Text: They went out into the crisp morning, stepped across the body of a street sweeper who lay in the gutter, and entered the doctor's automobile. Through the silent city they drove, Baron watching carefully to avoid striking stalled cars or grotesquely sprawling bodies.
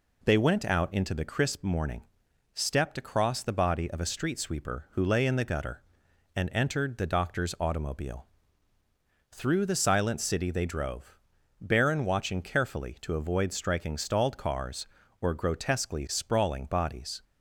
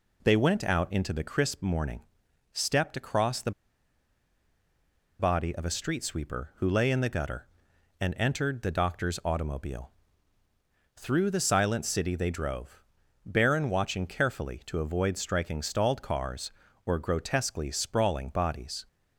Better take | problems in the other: first | pauses between "the" and "body"; strong; at 3.5 s; 1.6 s long

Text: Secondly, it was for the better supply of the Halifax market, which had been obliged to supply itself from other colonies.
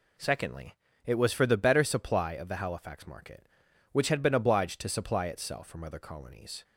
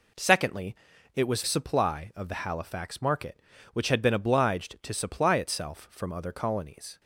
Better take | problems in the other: first | skips "for the better"; at 1.4 s

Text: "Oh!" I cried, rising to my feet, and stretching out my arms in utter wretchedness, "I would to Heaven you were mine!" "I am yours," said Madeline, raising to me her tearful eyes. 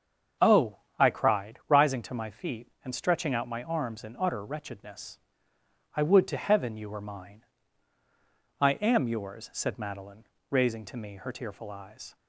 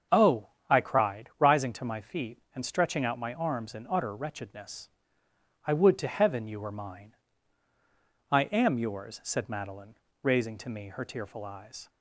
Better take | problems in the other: neither | starts louder than the rest; the same in both

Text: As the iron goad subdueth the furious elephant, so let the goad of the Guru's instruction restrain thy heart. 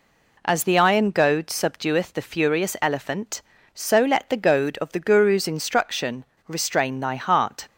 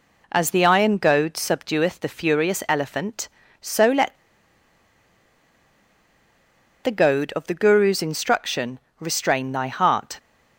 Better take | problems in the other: first | pauses between "let" and "the"; strong; at 4.1 s; 2.6 s long // pauses between "instruction" and "restrain"; slight; at 8.7 s; 0.20 s long; slight in the first

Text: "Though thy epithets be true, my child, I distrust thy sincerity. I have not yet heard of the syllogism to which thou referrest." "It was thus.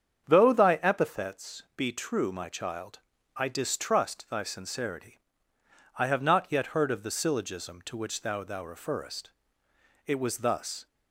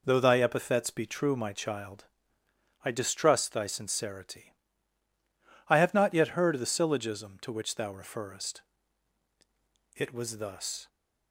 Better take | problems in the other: second | starts louder than the rest; strong; until 1.2 s; 8 dB // says "thou" twice; at 8.4 s

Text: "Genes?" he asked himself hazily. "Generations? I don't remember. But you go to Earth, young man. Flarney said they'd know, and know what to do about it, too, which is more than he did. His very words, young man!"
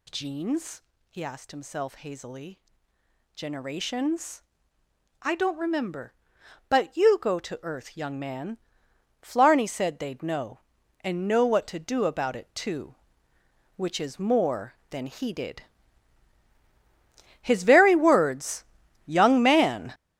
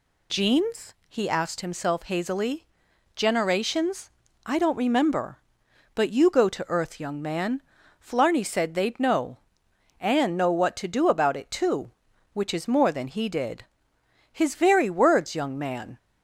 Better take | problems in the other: second | gets louder; strong; throughout; 10 dB

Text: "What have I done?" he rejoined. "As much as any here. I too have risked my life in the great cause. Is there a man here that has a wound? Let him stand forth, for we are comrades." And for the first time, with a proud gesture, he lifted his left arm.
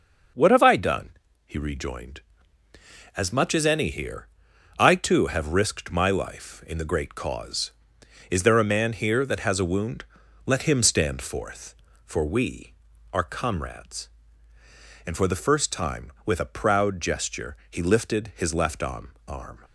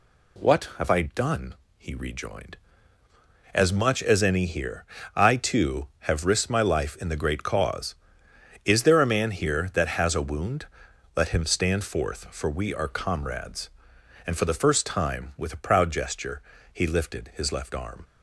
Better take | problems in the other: second | starts louder than the rest; until 1.7 s; 6 dB // says "arm" twice; at 19.2 s

